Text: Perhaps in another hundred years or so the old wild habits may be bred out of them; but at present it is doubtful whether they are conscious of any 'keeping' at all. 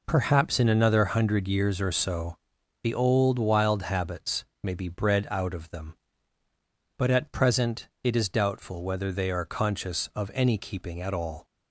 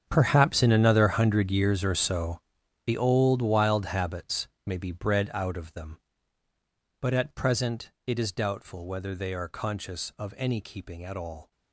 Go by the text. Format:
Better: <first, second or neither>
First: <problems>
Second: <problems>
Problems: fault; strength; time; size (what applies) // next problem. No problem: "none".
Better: first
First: pauses between "so" and "the"; noticeable; at 2.3 s; 0.46 s long // pauses between "habits" and "may"; slight; at 4.4 s; 0.16 s long // pauses between "present" and "it"; slight; at 7.8 s; 0.16 s long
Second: gets quieter; strong; throughout; 16 dB // pauses between "so" and "the"; noticeable; at 2.4 s; 0.46 s long // pauses between "habits" and "may"; slight; at 4.4 s; 0.16 s long // pauses between "present" and "it"; slight; at 7.9 s; 0.16 s long